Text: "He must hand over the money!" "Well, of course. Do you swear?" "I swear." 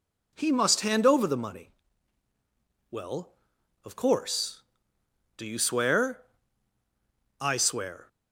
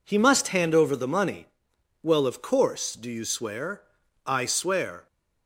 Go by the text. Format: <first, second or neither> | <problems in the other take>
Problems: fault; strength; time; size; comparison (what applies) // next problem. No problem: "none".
neither | none